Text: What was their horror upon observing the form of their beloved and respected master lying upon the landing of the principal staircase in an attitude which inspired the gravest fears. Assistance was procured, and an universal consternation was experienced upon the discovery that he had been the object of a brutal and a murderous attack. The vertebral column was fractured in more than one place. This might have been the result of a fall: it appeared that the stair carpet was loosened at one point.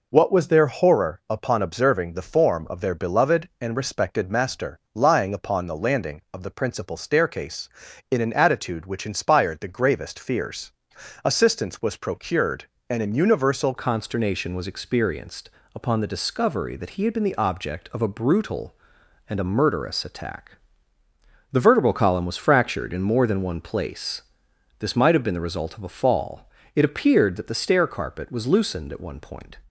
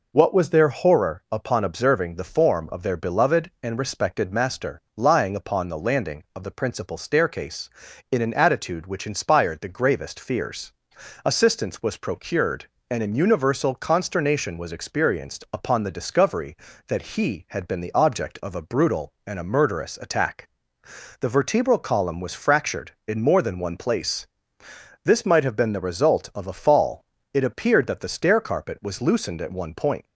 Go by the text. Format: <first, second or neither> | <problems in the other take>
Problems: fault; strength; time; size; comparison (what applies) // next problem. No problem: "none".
second | pauses between "master" and "lying"; slight; at 4.7 s; 0.16 s long; slight in the second // changes voice at "consternation"; from 13.7 s on; 15.8 s long // pauses between "experienced" and "upon"; slight; at 15.4 s; 0.26 s long